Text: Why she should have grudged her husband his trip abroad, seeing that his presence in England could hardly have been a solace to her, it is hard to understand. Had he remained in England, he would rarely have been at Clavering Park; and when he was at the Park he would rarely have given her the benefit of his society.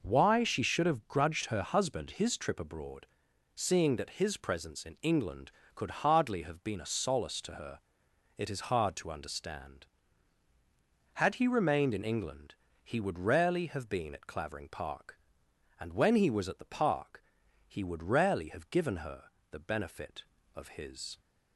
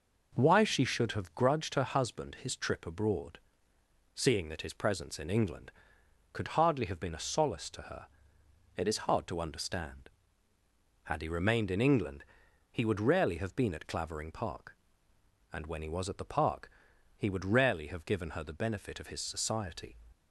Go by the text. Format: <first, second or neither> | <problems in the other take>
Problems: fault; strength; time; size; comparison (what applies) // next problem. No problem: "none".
second | pauses between "Park" and "he"; at 17.2 s; 0.44 s long; noticeable in the second // pauses between "her" and "the"; slight; at 19.2 s; 0.22 s long // stops before "society"; at 21.1 s